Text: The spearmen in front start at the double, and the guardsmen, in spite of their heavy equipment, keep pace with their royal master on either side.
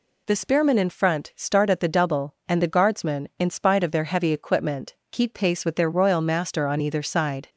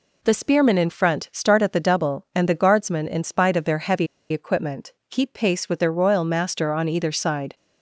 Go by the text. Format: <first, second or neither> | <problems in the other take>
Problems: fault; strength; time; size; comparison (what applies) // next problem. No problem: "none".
first | pauses between "heavy" and "equipment"; slight; at 4.0 s; 0.24 s long